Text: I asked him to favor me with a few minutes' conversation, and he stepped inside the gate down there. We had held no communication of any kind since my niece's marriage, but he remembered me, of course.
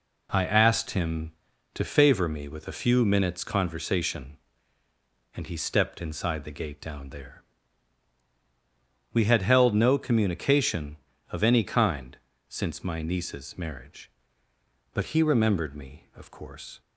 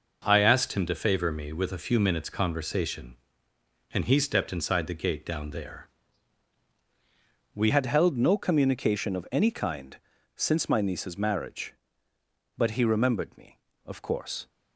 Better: first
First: pauses between "kind" and "since"; slight; at 12.1 s; 0.32 s long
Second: changes voice at "had"; from 7.6 s on; 6.8 s long // pauses between "kind" and "since"; at 9.9 s; 0.38 s long

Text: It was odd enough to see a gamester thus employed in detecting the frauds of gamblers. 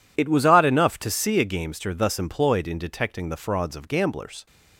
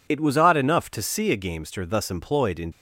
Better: first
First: none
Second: stops before "detecting the frauds of gamblers"; at 2.7 s

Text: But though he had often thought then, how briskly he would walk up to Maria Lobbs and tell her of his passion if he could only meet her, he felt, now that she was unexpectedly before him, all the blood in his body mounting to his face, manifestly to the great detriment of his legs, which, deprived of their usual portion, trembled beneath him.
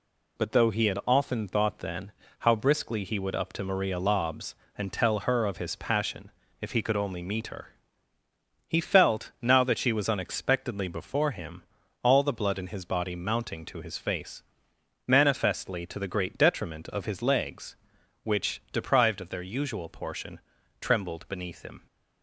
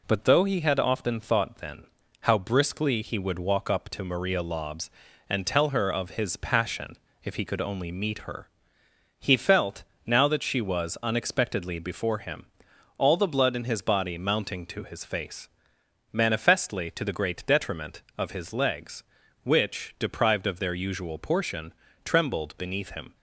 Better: second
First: skips "walk"; at 3.3 s // pauses between "passion" and "if"; slight; at 6.3 s; 0.30 s long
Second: pauses between "passion" and "if"; slight; at 6.9 s; 0.26 s long

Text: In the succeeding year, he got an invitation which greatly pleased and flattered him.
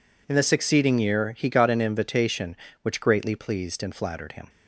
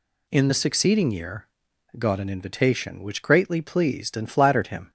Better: first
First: none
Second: skips "he"; at 1.7 s

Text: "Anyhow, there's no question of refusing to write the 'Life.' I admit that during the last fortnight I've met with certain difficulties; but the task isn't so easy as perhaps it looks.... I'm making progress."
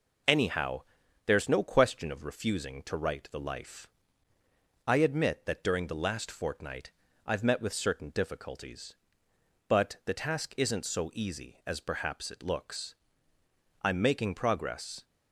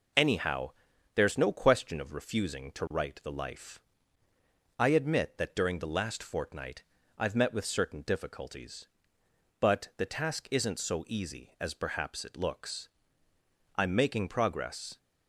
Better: neither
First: pauses between "fortnight" and "I've"; slight; at 6.9 s; 0.34 s long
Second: pauses between "fortnight" and "I've"; slight; at 6.8 s; 0.34 s long

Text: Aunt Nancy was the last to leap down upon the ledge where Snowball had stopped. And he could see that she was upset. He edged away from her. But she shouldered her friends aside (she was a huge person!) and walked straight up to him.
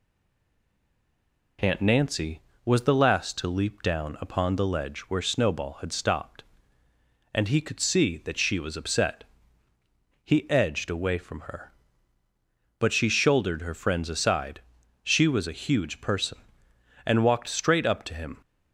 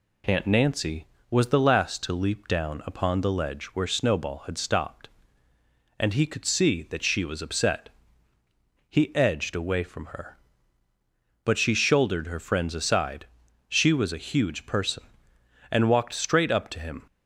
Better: second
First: stays silent before the first word; noticeable; until 1.5 s; 1.5 s long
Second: none

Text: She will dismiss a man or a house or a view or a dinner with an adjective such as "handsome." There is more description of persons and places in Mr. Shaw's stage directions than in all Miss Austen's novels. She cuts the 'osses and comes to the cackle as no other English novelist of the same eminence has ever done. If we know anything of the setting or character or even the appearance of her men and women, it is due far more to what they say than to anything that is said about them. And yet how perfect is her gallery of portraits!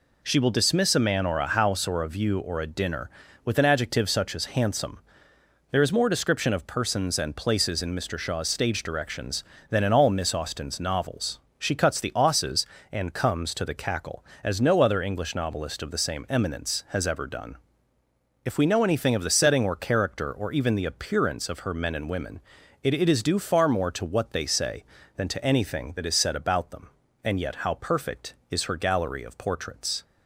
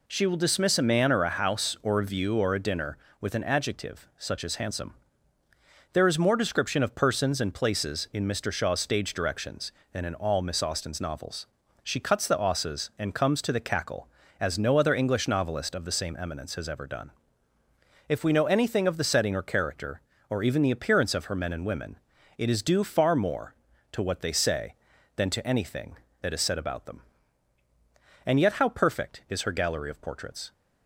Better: second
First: says "it" twice; at 22.9 s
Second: none

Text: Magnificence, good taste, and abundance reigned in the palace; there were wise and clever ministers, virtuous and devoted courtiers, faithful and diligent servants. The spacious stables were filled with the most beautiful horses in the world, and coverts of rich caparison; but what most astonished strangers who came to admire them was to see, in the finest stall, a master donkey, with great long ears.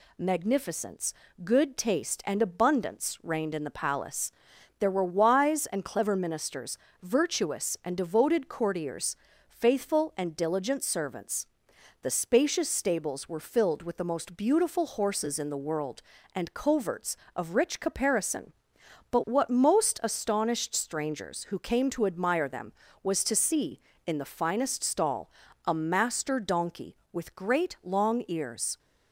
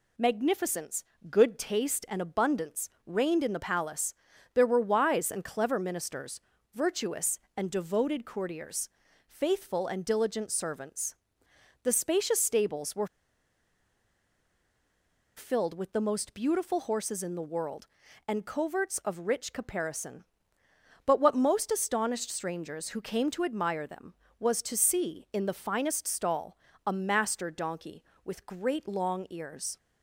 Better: first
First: none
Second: pauses between "abundance" and "reigned"; slight; at 2.9 s; 0.16 s long // pauses between "were" and "filled"; strong; at 13.0 s; 2.3 s long

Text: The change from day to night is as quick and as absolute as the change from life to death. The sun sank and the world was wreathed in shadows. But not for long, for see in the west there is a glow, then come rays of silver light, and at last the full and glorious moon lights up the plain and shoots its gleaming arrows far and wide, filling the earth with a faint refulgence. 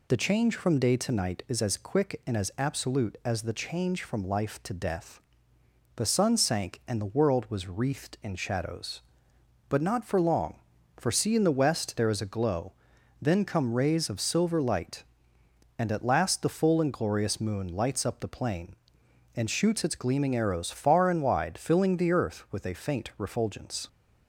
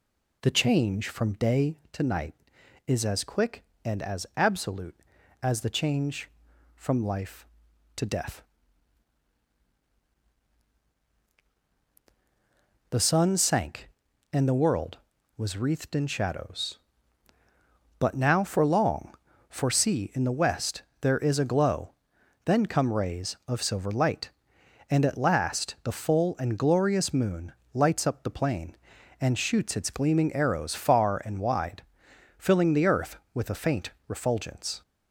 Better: first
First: none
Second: says "now" for "not"; at 18.1 s // pauses between "west" and "there"; slight; at 20.8 s; 0.20 s long // pauses between "moon" and "lights"; slight; at 27.5 s; 0.22 s long // pauses between "faint" and "refulgence"; slight; at 33.8 s; 0.18 s long

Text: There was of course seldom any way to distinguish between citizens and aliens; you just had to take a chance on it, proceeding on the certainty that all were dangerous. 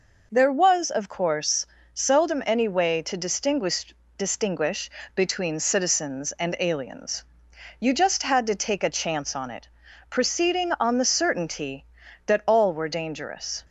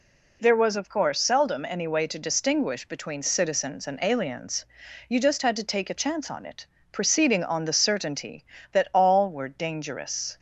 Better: second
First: pauses between "course" and "seldom"; slight; at 1.6 s; 0.26 s long // says "distinguish" twice; at 4.1 s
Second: none

